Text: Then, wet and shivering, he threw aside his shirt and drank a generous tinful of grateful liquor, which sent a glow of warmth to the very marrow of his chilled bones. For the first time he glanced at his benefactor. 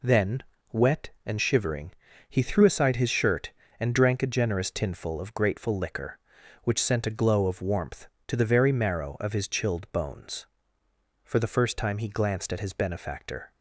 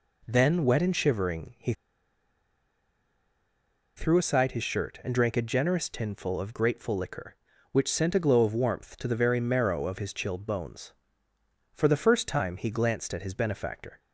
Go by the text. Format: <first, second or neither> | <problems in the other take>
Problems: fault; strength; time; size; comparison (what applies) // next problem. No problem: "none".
first | pauses between "he" and "threw"; strong; at 1.7 s; 2.2 s long